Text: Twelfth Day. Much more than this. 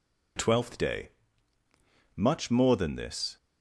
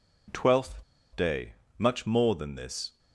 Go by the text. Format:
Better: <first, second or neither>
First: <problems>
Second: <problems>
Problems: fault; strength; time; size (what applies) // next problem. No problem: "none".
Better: first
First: none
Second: pauses between "Twelfth" and "Day"; slight; at 0.8 s; 0.30 s long